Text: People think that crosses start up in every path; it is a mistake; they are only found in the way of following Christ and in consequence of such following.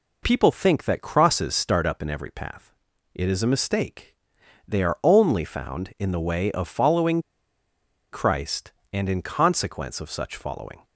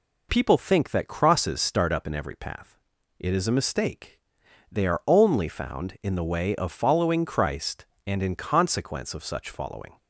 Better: second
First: pauses between "following" and "Christ"; noticeable; at 7.1 s; 0.92 s long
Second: none

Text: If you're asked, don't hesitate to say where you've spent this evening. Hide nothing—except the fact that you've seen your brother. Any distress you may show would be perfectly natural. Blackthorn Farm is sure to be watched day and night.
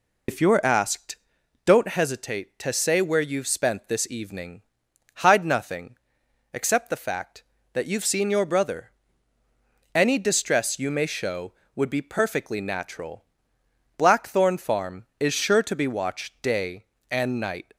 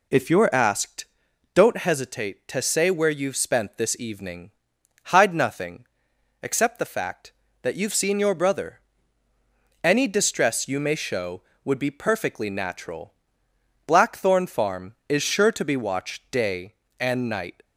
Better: second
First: loses the start of "If"; at 0.2 s; 75 ms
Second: none

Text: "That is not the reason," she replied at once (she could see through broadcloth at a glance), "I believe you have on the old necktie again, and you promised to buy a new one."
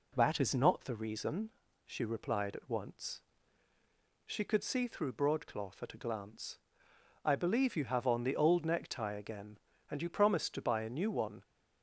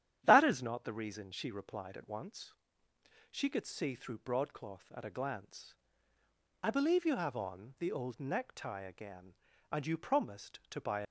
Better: first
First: none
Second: starts louder than the rest; strong; until 1.2 s; 10.5 dB // stops before "a new one"; at 11.0 s

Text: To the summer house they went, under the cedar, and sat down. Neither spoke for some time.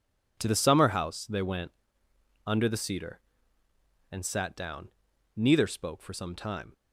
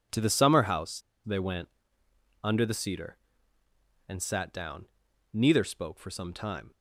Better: first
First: none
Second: pauses between "house" and "they"; slight; at 1.0 s; 0.25 s long

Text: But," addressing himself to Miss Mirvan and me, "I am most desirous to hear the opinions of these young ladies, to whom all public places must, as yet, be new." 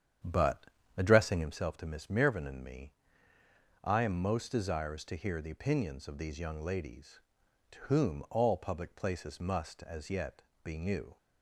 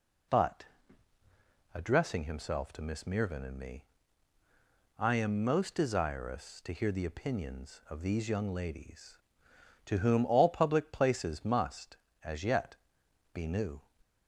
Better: second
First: starts louder than the rest; strong; until 1.6 s; 9 dB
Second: none

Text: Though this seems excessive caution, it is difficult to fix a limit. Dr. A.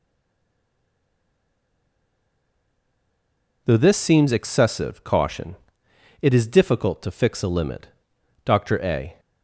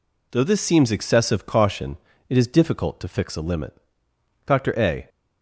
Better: second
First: stays silent before the first word; strong; until 3.6 s; 3.6 s long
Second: none

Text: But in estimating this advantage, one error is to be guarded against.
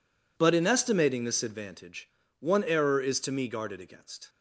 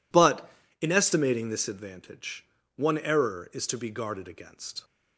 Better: second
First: says "me" for "be"; at 3.3 s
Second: none

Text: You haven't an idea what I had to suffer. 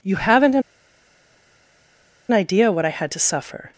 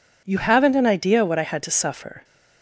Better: second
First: pauses between "an" and "idea"; strong; at 0.6 s; 1.7 s long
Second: none

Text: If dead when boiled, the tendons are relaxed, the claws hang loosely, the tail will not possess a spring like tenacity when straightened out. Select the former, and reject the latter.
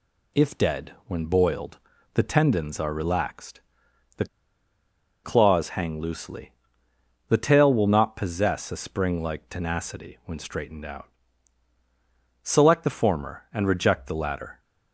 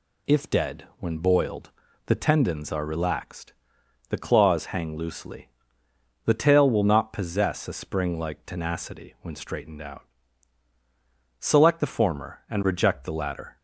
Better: second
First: pauses between "the" and "claws"; at 4.2 s; 0.98 s long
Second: none

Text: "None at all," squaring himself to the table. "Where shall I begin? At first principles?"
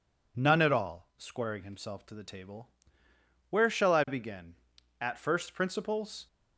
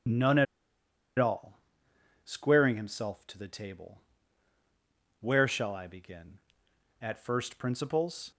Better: first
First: none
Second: starts louder than the rest; strong; until 2.4 s; 7 dB // pauses between "at" and "all"; noticeable; at 0.4 s; 0.73 s long

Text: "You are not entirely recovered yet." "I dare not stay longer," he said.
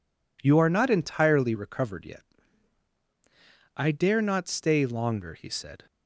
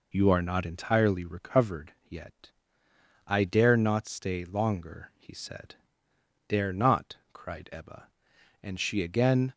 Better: first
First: none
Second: pauses between "recovered" and "yet"; slight; at 1.9 s; 0.16 s long // goes on to say "Dare not cried Ebba And she again"; strong; from 6.4 s on; 3.0 s long

